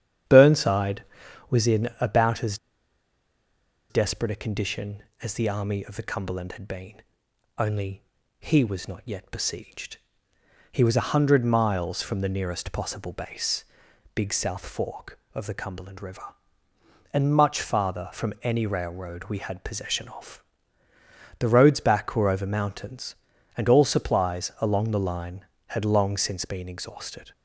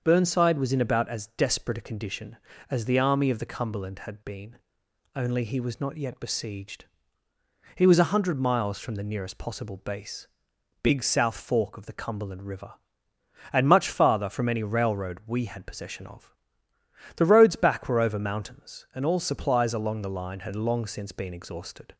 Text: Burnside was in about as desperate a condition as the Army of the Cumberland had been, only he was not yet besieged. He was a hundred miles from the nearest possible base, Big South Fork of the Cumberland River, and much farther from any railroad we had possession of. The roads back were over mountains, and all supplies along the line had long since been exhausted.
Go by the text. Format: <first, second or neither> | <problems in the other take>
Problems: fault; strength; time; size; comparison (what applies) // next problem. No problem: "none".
second | starts louder than the rest; strong; until 1.7 s; 9.5 dB; also in the second // pauses between "as" and "desperate"; strong; at 2.5 s; 1.3 s long // pauses between "only" and "he"; at 8.0 s; 0.38 s long